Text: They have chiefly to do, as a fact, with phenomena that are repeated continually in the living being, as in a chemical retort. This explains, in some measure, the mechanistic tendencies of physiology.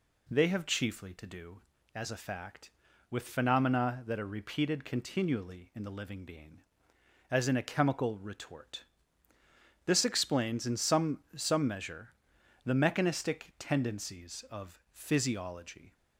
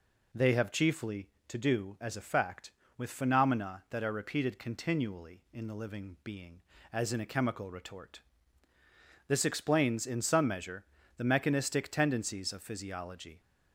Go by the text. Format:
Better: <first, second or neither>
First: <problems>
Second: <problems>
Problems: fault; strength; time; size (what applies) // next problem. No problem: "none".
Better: second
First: says "some" twice; at 11.3 s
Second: none